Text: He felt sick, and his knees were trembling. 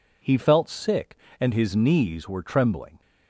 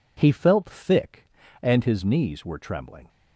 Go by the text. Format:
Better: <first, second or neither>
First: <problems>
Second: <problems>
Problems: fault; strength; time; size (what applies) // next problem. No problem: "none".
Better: first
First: none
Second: says "thick" for "sick"; at 0.6 s